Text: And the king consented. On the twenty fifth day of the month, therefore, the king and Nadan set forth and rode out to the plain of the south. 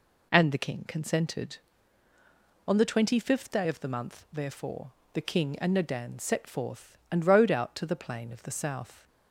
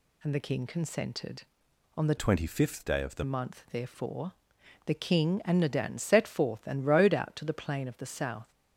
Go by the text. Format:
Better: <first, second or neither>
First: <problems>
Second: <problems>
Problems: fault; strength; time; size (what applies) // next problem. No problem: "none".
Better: first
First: none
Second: changes voice from "twenty" to "the"; from 2.1 to 3.2 s; 1.1 s long